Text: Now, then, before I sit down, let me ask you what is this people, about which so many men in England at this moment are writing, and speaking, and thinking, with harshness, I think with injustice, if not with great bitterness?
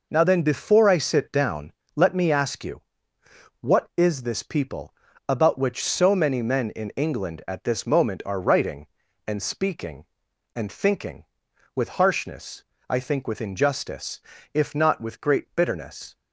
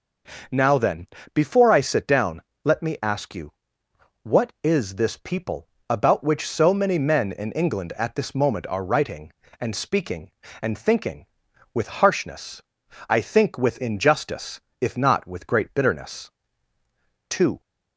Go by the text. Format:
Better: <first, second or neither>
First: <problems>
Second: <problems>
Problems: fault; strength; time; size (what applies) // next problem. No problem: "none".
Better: first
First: pauses between "you" and "what"; noticeable; at 2.8 s; 0.80 s long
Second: starts louder than the rest; noticeable; until 1.7 s; 6 dB // pauses between "you" and "what"; noticeable; at 3.5 s; 0.70 s long // goes on to say "Two"; slight; from 17.2 s on; 0.30 s long